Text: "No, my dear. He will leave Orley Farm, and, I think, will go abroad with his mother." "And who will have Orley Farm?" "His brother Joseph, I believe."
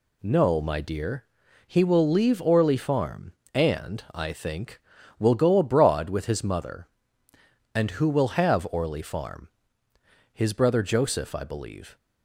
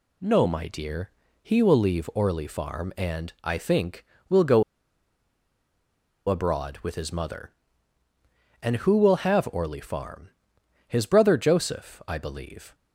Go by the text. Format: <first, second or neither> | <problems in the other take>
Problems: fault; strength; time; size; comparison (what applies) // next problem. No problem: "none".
first | pauses between "go" and "abroad"; strong; at 4.6 s; 1.6 s long